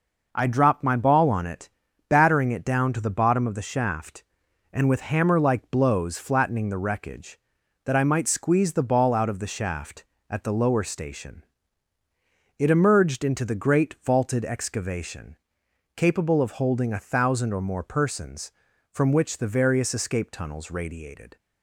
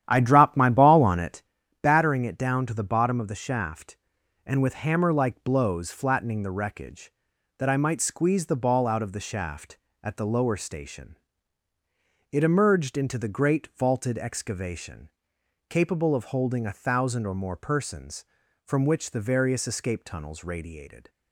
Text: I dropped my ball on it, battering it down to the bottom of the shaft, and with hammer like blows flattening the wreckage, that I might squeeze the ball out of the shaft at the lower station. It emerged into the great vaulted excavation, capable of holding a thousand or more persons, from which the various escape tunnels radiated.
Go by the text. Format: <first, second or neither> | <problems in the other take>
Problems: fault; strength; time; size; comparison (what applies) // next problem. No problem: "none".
first | starts louder than the rest; strong; until 1.5 s; 11 dB